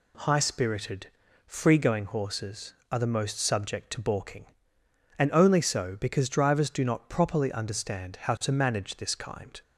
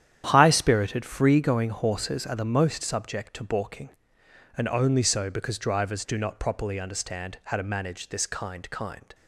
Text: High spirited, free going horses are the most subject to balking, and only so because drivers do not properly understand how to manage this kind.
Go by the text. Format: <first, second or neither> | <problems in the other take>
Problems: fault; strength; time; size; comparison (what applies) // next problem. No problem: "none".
first | starts louder than the rest; strong; until 1.2 s; 10 dB // says "kind" twice; at 8.6 s